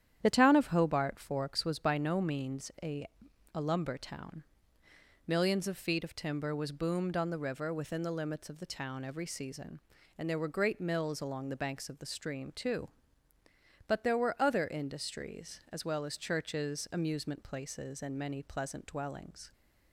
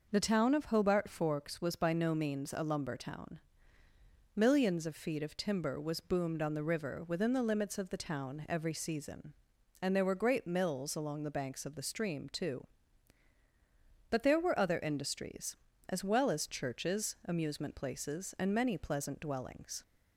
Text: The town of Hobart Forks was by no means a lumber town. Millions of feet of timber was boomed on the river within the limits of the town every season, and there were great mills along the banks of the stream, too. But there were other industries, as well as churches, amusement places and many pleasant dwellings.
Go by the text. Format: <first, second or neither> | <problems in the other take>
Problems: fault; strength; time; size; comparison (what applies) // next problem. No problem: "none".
second | starts louder than the rest; strong; until 1.2 s; 10 dB // says "a" twice; at 3.5 s